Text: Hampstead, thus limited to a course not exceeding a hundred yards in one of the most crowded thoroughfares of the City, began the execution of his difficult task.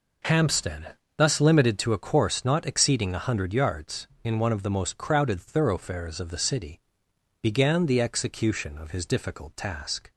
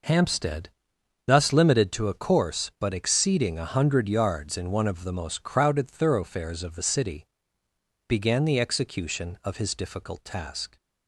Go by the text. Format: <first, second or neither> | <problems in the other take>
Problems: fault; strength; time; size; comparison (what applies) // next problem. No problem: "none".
first | says "but" for "not"; at 2.7 s